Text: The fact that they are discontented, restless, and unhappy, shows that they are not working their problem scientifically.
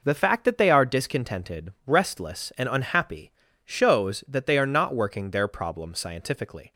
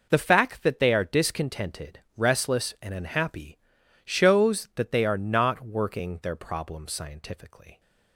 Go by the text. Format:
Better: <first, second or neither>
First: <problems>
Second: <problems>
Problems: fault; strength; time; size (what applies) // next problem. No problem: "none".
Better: neither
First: none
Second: none